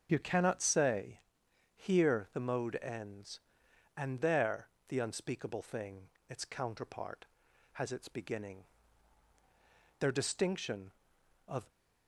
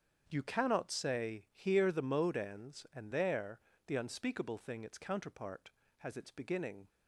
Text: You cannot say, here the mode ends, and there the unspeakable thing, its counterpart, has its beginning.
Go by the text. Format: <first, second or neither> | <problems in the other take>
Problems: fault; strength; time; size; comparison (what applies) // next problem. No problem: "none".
second | starts louder than the rest; strong; until 1.1 s; 7.5 dB; strong in the second // pauses between "there" and "the"; slight; at 4.6 s; 0.22 s long; slight in the second // goes on to say "Their distinction of"; strong; from 9.9 s on; 1.7 s long